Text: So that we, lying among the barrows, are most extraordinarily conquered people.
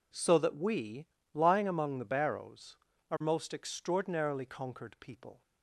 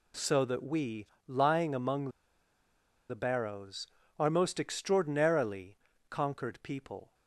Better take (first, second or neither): first